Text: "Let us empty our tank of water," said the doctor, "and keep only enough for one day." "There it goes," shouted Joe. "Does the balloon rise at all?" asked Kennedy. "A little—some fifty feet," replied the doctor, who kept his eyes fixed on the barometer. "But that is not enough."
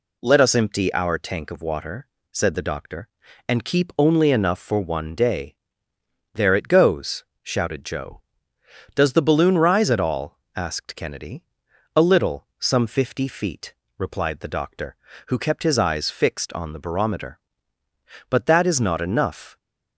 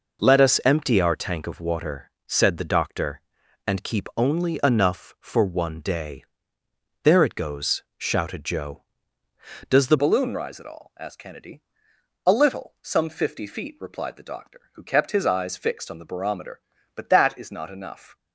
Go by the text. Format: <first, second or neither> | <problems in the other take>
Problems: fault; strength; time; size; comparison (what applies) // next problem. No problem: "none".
first | changes voice at "balloon"; from 9.9 s on; 8.2 s long